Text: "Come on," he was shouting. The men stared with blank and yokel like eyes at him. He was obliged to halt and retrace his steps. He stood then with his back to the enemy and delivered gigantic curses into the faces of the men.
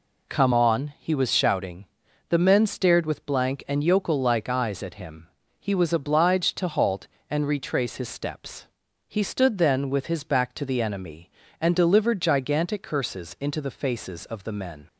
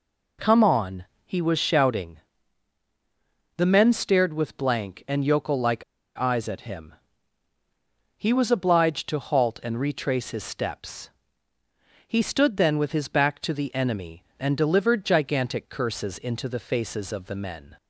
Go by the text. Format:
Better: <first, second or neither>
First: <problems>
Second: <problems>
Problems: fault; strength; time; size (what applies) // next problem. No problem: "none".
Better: first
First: none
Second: pauses between "like" and "eyes"; slight; at 5.8 s; 0.34 s long